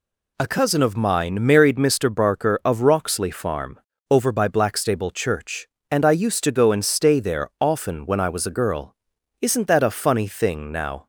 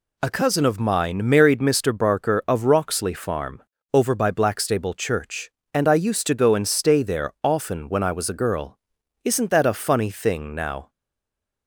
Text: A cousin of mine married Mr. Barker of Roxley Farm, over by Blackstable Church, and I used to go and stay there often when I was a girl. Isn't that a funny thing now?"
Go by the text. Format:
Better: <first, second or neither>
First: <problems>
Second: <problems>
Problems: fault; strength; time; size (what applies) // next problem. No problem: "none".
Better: first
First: none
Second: stays silent after the last word; slight; from 10.8 s on; 0.8 s long